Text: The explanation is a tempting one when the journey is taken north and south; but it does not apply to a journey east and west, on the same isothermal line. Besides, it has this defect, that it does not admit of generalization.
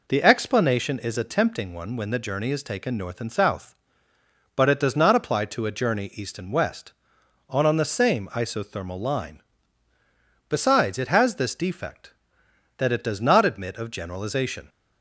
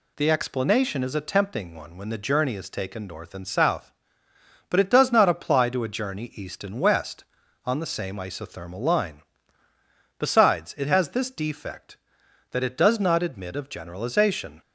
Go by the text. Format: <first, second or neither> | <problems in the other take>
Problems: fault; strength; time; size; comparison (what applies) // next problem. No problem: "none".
second | says "on" twice; at 7.6 s